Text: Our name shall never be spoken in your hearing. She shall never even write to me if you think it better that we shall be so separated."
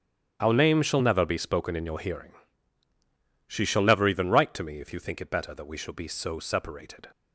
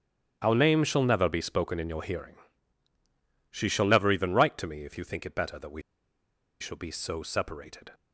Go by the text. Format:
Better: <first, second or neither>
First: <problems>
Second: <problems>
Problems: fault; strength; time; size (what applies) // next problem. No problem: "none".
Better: first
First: starts louder than the rest; strong; until 1.3 s; 10 dB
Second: starts louder than the rest; strong; until 1.4 s; 10.5 dB // pauses between "we" and "shall"; noticeable; at 5.8 s; 0.79 s long